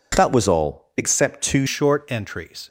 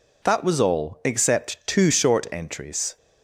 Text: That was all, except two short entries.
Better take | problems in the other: second | changes voice at "short"; from 1.6 s on; 1.0 s long

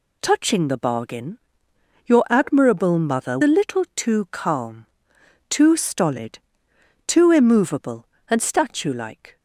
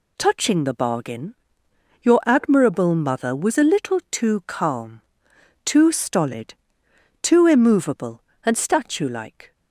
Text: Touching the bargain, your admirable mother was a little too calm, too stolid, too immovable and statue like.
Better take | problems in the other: second | skips "was"; at 3.4 s

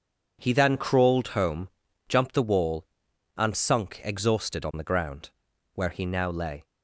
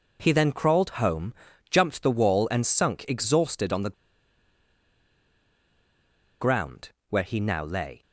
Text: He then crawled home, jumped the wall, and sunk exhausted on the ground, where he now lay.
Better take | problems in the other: first | pauses between "the" and "ground"; strong; at 3.9 s; 2.4 s long

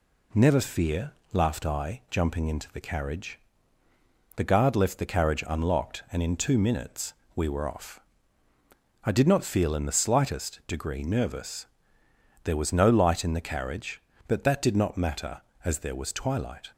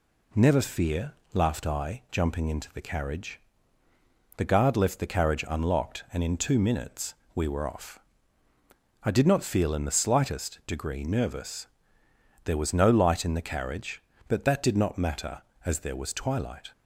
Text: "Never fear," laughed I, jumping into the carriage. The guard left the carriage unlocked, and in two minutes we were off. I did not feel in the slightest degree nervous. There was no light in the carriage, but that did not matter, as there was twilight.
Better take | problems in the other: neither | pauses between "minutes" and "we"; slight; the same in both

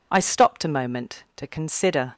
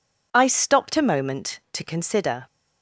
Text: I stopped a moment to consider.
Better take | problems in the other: neither | none

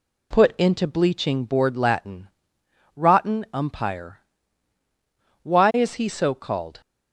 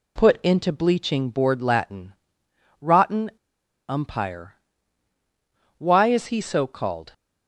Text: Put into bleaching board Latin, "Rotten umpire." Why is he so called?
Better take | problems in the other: first | pauses between "Rotten" and "umpire"; noticeable; at 3.2 s; 0.59 s long

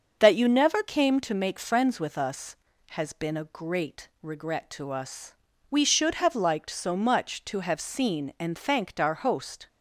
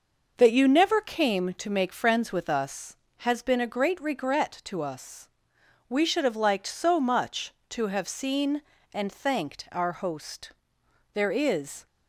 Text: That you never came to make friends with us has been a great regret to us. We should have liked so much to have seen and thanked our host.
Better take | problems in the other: first | starts louder than the rest; noticeable; until 1.3 s; 6 dB; also in the first // goes on to say "There is"; noticeable; from 11.1 s on; 0.72 s long

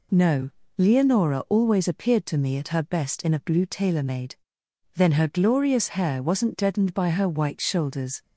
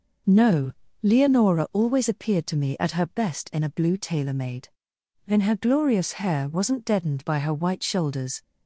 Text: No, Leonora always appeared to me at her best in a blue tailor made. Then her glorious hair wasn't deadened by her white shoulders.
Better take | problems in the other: neither | none

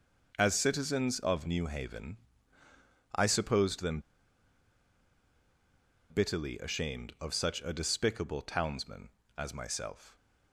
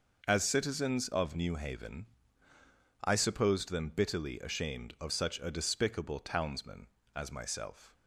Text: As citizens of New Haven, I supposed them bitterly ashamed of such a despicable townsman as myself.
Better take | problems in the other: second | pauses between "them" and "bitterly"; strong; at 3.9 s; 2.1 s long

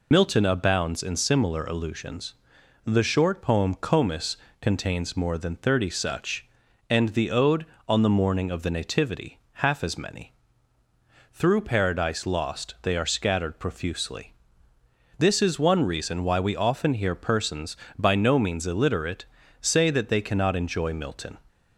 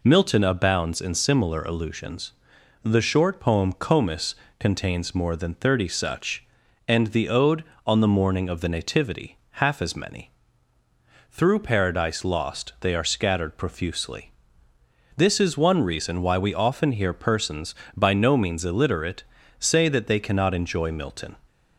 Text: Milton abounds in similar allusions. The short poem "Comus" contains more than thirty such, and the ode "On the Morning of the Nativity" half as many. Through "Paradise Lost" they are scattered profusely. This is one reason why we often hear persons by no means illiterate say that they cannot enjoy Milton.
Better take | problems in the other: second | loses the start of "Milton"; at 0.1 s; 65 ms // pauses between "Comus" and "contains"; slight; at 4.3 s; 0.26 s long; slight in the second // pauses between "Nativity" and "half"; slight; at 9.3 s; 0.26 s long; slight in the second // pauses between "illiterate" and "say"; slight; at 19.2 s; 0.36 s long; slight in the second

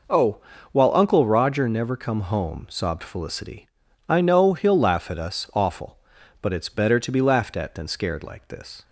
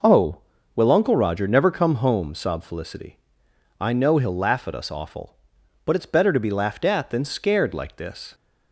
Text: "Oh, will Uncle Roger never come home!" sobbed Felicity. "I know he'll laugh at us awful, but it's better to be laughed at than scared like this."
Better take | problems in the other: second | says "while" for "will"; at 0.7 s

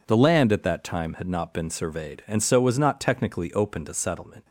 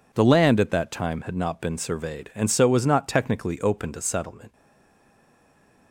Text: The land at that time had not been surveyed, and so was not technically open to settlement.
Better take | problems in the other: first | stays silent after the last word; noticeable; from 4.5 s on; 1.4 s long

